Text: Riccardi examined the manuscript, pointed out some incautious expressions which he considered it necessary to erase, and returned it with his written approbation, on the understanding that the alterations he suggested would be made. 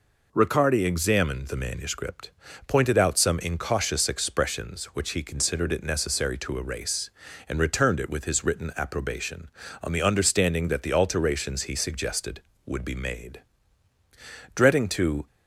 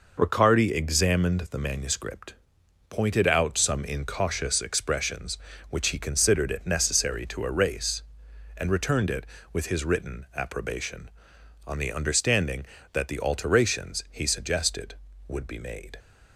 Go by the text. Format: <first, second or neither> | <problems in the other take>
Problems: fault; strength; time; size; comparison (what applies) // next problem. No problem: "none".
second | goes on to say "Dreading to"; noticeable; from 14.5 s on; 0.72 s long